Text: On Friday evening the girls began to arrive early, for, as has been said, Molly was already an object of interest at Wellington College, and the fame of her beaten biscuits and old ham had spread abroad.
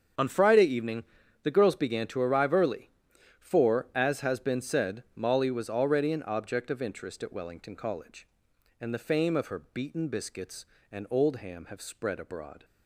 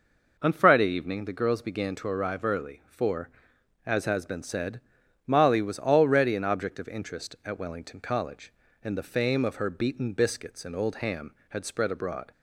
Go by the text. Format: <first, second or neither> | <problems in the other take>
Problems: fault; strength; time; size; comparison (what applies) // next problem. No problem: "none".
second | starts louder than the rest; strong; until 1.5 s; 7 dB // pauses between "evening" and "the"; slight; at 1.0 s; 0.36 s long // says "have" for "had"; at 11.6 s